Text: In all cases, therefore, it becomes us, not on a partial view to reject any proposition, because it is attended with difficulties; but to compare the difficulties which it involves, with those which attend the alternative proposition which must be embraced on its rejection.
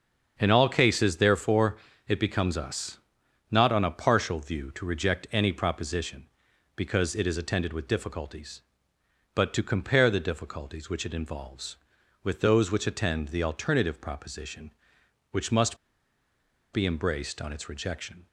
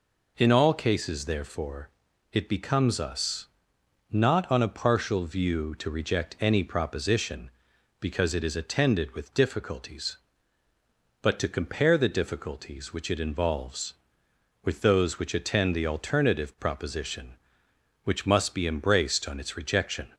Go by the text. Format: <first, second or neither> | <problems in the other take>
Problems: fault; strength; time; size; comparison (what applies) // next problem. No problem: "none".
second | starts louder than the rest; until 1.3 s; 7 dB // pauses between "must" and "be"; at 15.7 s; 0.98 s long